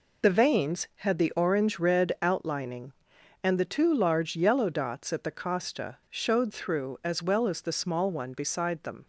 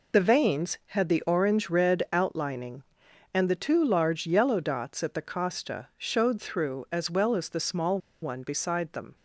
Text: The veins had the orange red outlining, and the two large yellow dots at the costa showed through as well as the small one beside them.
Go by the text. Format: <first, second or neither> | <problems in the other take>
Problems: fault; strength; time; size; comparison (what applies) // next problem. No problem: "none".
first | pauses between "small" and "one"; slight; at 7.9 s; 0.24 s long